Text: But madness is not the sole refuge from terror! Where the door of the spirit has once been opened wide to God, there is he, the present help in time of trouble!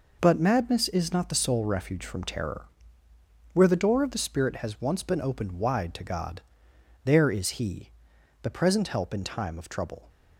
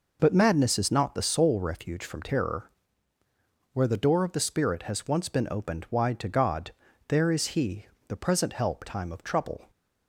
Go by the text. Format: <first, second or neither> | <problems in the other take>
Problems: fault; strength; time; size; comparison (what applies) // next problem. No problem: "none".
first | skips "in"; at 8.8 s